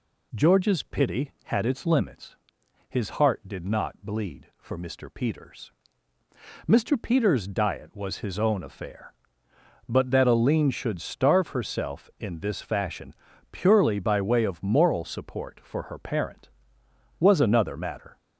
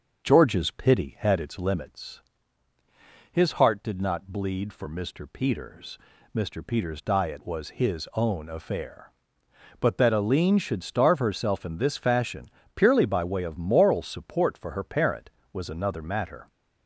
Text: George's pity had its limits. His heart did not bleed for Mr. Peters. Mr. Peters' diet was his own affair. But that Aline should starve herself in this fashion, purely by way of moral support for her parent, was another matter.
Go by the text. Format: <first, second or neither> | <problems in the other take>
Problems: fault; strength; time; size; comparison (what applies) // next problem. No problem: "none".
first | starts louder than the rest; until 1.9 s; 6.5 dB